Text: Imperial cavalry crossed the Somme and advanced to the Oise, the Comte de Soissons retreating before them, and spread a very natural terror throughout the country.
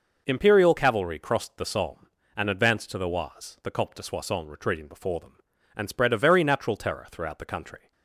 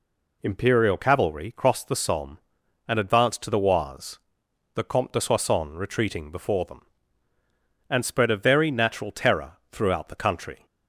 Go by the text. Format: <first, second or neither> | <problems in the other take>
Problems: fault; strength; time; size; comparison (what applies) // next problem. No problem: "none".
neither | none